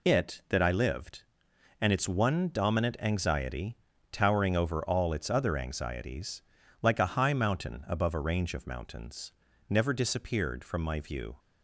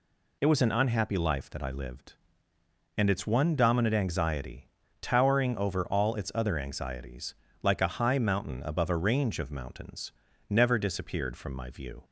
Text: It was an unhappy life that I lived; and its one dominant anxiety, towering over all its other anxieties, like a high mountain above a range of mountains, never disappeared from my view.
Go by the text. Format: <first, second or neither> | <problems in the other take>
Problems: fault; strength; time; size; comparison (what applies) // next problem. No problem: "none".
second | skips "was an unhappy life"; at 0.4 s